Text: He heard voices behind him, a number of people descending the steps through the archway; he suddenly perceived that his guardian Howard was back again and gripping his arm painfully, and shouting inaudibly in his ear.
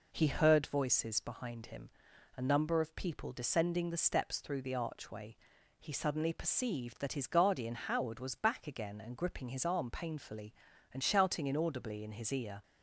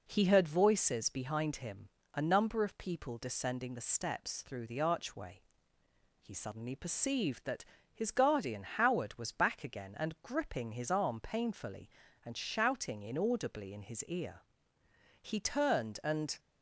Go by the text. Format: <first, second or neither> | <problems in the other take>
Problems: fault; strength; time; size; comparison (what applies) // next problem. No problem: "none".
first | pauses between "that" and "his"; slight; at 7.6 s; 0.28 s long // goes on to say "He turned and"; noticeable; from 15.2 s on; 1.1 s long